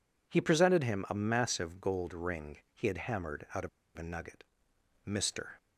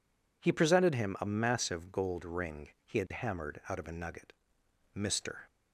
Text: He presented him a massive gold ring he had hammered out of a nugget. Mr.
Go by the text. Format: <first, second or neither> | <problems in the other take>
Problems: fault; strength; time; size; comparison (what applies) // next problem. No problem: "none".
second | pauses between "ring" and "he"; slight; at 2.5 s; 0.16 s long; slight in the second // pauses between "of" and "a"; slight; at 3.6 s; 0.28 s long